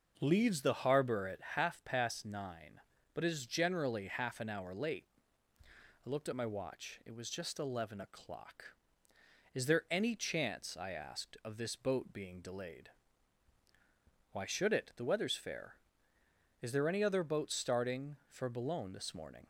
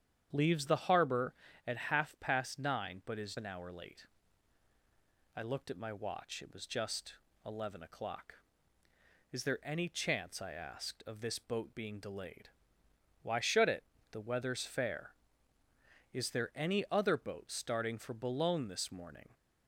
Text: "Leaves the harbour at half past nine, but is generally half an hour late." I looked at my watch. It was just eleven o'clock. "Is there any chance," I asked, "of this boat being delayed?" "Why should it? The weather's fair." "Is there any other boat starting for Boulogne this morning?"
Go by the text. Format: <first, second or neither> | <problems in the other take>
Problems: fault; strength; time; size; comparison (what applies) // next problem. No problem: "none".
first | starts louder than the rest; strong; until 1.3 s; 9 dB // skips "generally half"; at 3.3 s // pauses between "just" and "eleven"; slight; at 7.1 s; 0.30 s long